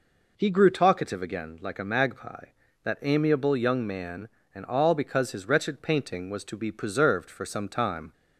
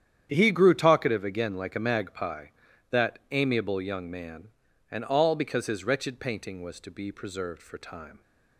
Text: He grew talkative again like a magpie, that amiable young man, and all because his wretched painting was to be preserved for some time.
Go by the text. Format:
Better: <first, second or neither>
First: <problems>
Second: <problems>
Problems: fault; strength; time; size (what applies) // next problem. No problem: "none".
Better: first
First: none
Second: starts louder than the rest; strong; until 1.3 s; 9.5 dB // skips "some"; at 7.7 s